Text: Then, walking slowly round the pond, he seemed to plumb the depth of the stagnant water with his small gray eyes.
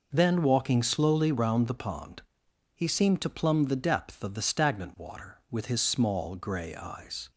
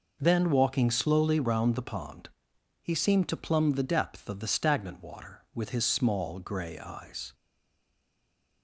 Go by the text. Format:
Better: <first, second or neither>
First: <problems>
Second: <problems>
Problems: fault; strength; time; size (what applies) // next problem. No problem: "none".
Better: first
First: none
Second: stays silent after the last word; noticeable; from 7.3 s on; 1.3 s long